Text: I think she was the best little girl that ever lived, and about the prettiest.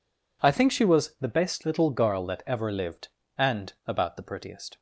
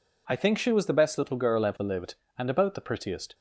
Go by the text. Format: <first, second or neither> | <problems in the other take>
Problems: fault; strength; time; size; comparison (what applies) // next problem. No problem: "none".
first | skips "that"; at 1.6 s